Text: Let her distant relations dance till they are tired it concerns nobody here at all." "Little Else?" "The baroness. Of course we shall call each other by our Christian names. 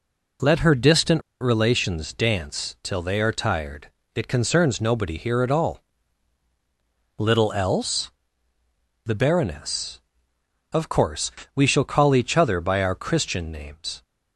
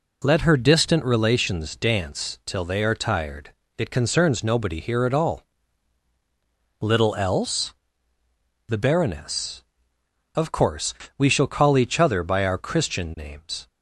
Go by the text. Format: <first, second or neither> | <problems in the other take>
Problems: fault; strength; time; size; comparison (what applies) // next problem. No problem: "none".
second | pauses between "distant" and "relations"; slight; at 1.2 s; 0.19 s long // pauses between "tired" and "it"; slight; at 3.8 s; 0.26 s long; slight in the second // pauses between "course" and "we"; slight; at 11.3 s; 0.24 s long; slight in the second